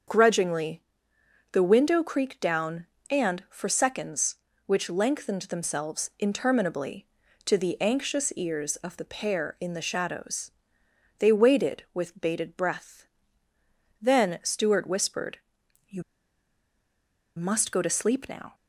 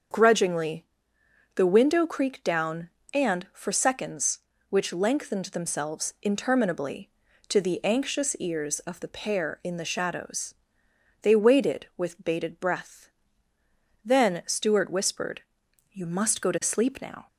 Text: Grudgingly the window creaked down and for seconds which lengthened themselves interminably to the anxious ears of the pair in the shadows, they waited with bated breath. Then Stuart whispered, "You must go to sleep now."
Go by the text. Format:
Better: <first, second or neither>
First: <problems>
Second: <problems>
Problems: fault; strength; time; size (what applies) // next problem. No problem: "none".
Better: second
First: starts louder than the rest; until 1.7 s; 7 dB // pauses between "Grudgingly" and "the"; noticeable; at 0.8 s; 0.70 s long // pauses between "You" and "must"; strong; at 16.0 s; 1.3 s long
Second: starts louder than the rest; until 1.8 s; 7 dB // pauses between "Grudgingly" and "the"; noticeable; at 0.8 s; 0.70 s long